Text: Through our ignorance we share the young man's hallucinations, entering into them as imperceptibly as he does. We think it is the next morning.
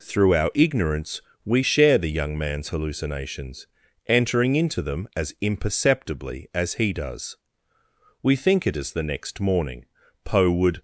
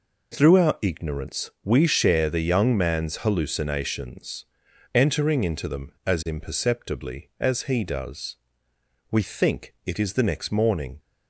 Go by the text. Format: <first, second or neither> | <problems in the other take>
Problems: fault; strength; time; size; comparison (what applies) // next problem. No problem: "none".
second | pauses between "ignorance" and "we"; slight; at 1.2 s; 0.24 s long // goes on to say "Poe would"; from 10.2 s on; 0.58 s long